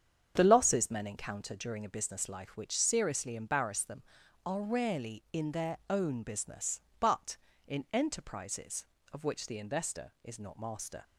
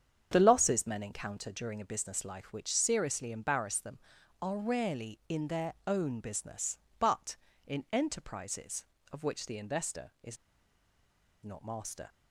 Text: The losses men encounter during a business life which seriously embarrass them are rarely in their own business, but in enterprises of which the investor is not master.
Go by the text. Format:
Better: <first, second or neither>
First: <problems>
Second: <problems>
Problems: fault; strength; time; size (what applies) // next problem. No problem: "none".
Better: first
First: starts louder than the rest; strong; until 1.3 s; 8 dB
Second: starts louder than the rest; strong; until 1.3 s; 8 dB // pauses between "is" and "not"; at 10.3 s; 1.0 s long